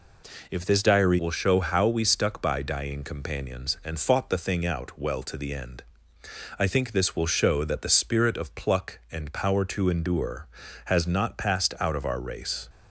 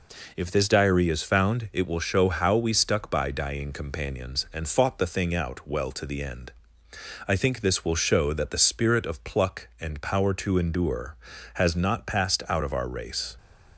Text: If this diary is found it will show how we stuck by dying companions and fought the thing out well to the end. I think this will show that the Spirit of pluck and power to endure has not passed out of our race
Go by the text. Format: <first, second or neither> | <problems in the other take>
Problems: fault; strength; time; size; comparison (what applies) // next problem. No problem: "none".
second | skips "is found it"; at 1.1 s